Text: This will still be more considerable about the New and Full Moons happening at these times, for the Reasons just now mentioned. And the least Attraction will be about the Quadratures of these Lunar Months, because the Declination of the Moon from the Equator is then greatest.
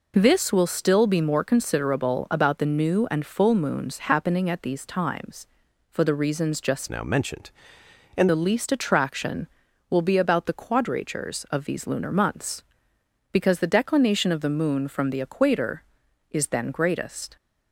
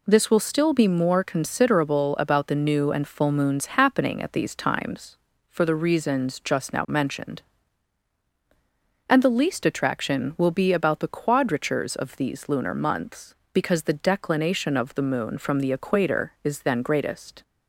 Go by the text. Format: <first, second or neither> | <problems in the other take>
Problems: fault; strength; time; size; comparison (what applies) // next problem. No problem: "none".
second | changes voice from "now" to "And"; from 6.8 to 8.2 s; 1.4 s long